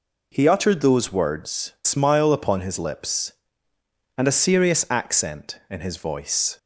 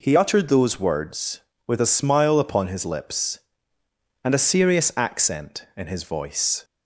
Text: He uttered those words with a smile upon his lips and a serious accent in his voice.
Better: second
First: skips "with a"; at 1.8 s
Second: none

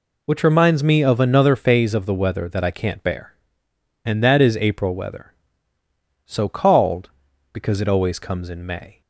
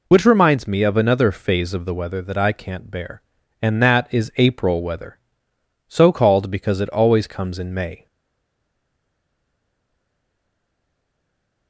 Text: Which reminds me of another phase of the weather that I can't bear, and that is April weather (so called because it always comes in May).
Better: first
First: none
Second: stays silent after the last word; strong; from 8.0 s on; 3.6 s long

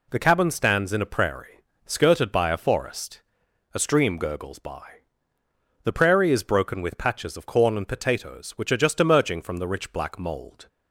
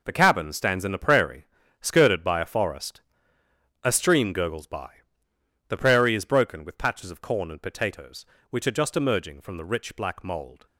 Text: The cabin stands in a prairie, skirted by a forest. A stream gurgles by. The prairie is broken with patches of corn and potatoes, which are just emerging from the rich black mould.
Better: first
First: none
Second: gets quieter; strong; throughout; 11.5 dB

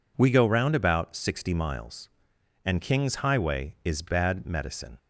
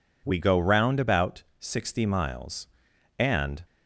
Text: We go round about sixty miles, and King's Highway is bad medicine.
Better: first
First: none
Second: pauses between "about" and "sixty"; slight; at 1.4 s; 0.18 s long // stops before "King's Highway is bad medicine"; at 3.6 s

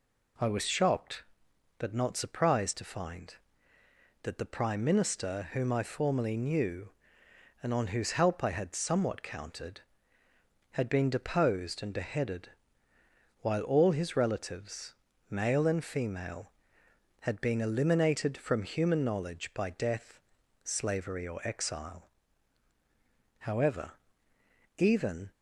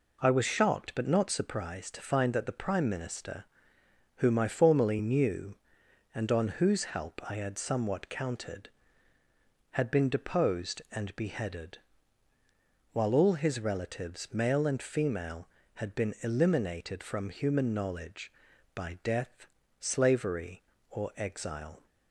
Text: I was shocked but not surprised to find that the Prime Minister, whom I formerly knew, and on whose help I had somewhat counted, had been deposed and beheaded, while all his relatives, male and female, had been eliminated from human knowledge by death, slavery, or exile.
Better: second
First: goes on to say "However even"; strong; from 23.4 s on; 1.9 s long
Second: none

